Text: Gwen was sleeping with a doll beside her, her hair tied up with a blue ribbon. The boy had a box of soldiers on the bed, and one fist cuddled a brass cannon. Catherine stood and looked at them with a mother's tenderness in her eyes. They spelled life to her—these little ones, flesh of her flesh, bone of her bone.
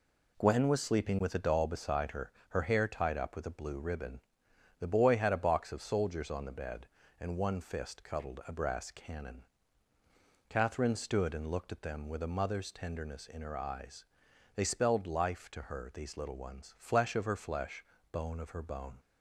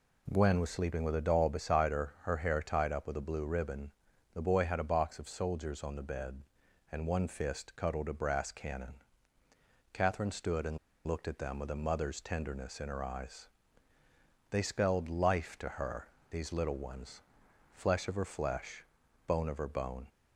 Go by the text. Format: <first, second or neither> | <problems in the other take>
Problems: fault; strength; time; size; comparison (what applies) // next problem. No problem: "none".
first | pauses between "and" and "looked"; slight; at 10.7 s; 0.29 s long